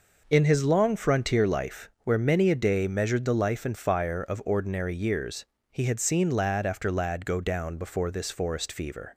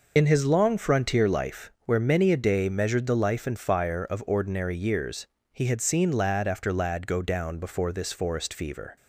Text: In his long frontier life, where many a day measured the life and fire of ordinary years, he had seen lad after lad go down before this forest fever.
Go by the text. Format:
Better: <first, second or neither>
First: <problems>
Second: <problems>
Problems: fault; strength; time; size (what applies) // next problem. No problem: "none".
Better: first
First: none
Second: loses the start of "In"; at 0.1 s; 90 ms